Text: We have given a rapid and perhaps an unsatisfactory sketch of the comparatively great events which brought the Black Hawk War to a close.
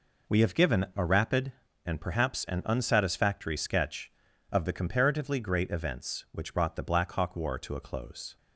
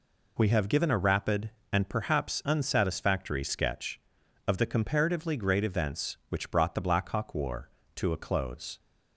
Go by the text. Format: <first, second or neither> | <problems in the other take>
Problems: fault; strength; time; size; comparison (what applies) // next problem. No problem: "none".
first | skips "an"; at 2.4 s